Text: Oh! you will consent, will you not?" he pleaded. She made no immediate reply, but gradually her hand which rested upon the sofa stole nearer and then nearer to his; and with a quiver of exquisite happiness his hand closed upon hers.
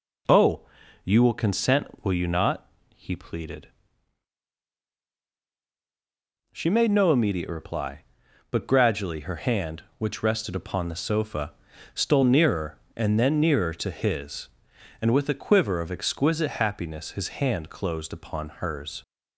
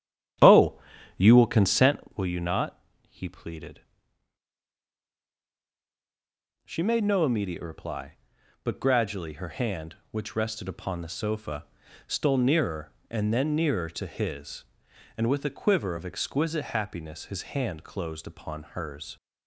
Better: first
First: pauses between "sofa" and "stole"; at 11.5 s; 0.40 s long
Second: starts louder than the rest; strong; until 1.9 s; 10.5 dB // pauses between "sofa" and "stole"; at 11.6 s; 0.40 s long

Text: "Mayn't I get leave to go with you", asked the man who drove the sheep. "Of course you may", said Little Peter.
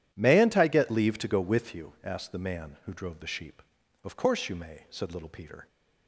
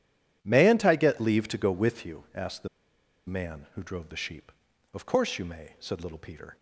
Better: first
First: none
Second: pauses between "the" and "man"; noticeable; at 2.6 s; 0.60 s long

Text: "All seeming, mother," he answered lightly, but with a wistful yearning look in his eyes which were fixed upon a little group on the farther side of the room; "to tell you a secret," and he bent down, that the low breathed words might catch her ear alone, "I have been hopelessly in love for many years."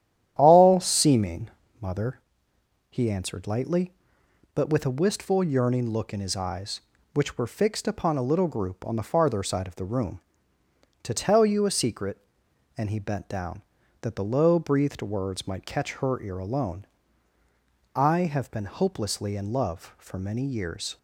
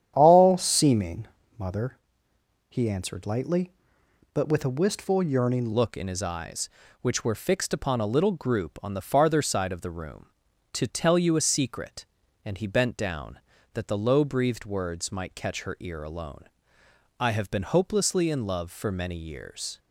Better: first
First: starts louder than the rest; strong; until 1.3 s; 11 dB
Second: starts louder than the rest; strong; until 1.1 s; 9.5 dB // changes voice at "look"; from 5.7 s on; 14.0 s long

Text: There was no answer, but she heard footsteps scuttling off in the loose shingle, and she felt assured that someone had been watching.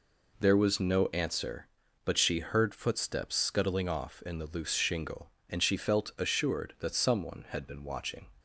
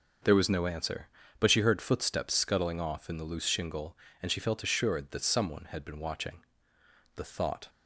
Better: first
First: none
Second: starts louder than the rest; until 1.5 s; 6.5 dB // goes on to say "The thought"; from 7.1 s on; 0.52 s long

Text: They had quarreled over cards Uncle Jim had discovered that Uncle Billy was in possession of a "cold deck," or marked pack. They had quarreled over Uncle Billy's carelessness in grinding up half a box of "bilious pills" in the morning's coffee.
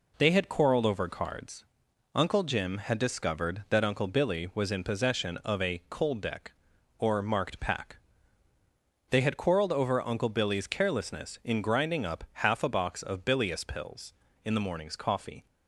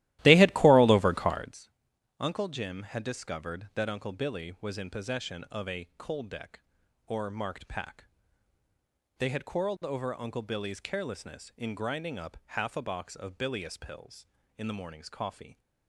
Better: first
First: pauses between "cards" and "Uncle"; noticeable; at 1.6 s; 0.50 s long // pauses between "up" and "half"; slight; at 12.2 s; 0.18 s long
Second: starts louder than the rest; strong; until 1.6 s; 15.5 dB // pauses between "cards" and "Uncle"; noticeable; at 1.6 s; 0.50 s long // pauses between "up" and "half"; slight; at 12.3 s; 0.18 s long

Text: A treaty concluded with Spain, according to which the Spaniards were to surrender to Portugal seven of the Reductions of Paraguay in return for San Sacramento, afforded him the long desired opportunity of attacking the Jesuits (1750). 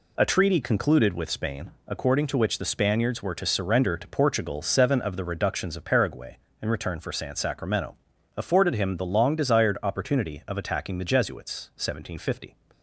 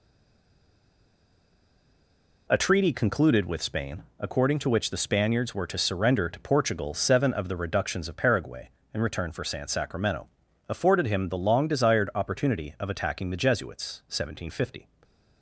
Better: first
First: none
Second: stays silent before the first word; until 2.4 s; 2.4 s long

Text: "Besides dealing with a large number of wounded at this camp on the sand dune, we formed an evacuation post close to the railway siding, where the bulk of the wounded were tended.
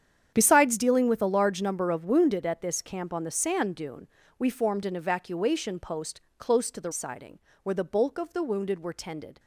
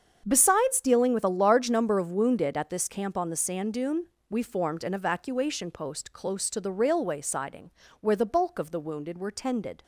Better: second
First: starts louder than the rest; strong; until 1.3 s; 8.5 dB // pauses between "post" and "close"; slight; at 6.2 s; 0.18 s long // skips "railway"; at 6.9 s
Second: starts louder than the rest; until 1.2 s; 7 dB

